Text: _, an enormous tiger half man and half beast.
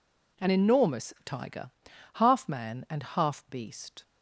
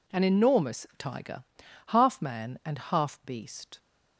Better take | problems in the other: neither | pauses between "tiger" and "half"; the same in both

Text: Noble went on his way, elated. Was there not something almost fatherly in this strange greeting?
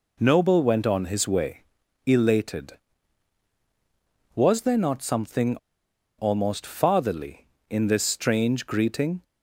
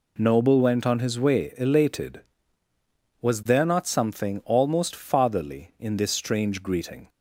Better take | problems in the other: second | pauses between "something" and "almost"; noticeable; at 5.5 s; 0.61 s long

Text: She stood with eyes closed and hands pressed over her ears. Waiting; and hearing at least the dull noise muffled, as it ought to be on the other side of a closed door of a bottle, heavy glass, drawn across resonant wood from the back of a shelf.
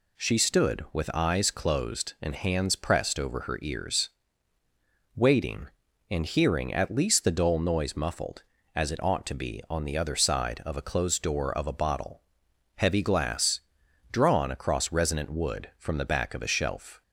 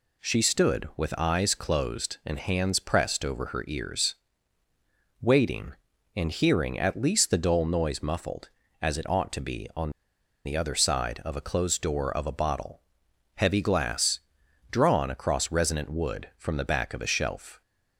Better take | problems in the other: first | pauses between "on" and "the"; noticeable; at 9.9 s; 0.55 s long

